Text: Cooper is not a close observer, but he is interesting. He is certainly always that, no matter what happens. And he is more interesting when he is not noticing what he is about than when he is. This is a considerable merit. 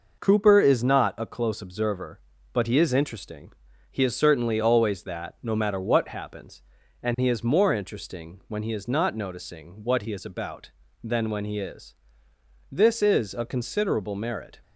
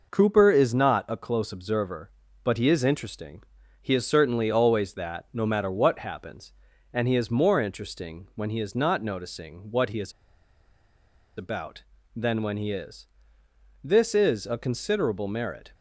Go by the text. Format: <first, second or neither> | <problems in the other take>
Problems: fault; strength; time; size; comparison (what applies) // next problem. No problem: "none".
first | pauses between "is" and "about"; strong; at 10.1 s; 1.2 s long